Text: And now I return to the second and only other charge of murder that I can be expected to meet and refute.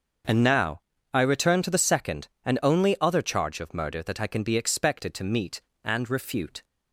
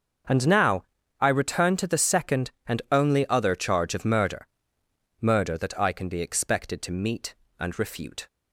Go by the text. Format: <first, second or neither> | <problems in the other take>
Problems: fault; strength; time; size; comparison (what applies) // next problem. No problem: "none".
first | starts louder than the rest; until 1.6 s; 6.5 dB; also in the first // pauses between "now" and "I"; slight; at 0.8 s; 0.36 s long; slight in the first // says "murder" twice; at 5.2 s